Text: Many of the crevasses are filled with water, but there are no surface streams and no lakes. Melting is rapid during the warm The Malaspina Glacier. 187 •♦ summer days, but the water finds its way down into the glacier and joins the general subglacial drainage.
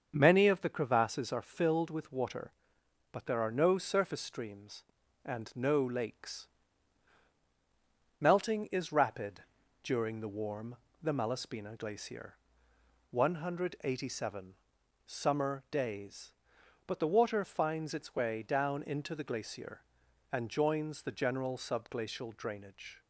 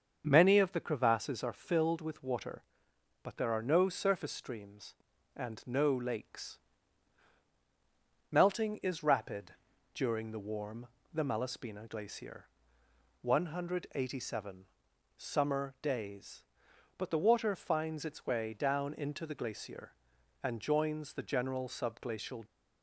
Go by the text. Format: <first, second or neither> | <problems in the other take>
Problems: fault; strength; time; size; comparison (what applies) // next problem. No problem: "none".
first | starts louder than the rest; until 1.2 s; 6.5 dB; also in the first // pauses between "rapid" and "during"; at 9.5 s; 0.42 s long; also in the first // pauses between "warm" and "The"; slight; at 10.8 s; 0.26 s long; slight in the first // stops before "drainage"; at 22.4 s